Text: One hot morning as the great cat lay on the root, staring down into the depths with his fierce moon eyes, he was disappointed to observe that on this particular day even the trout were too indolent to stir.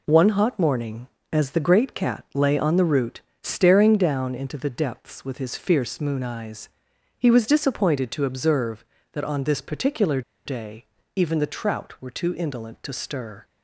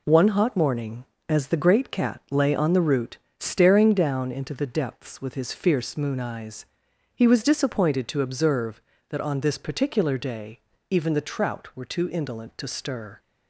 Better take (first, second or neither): second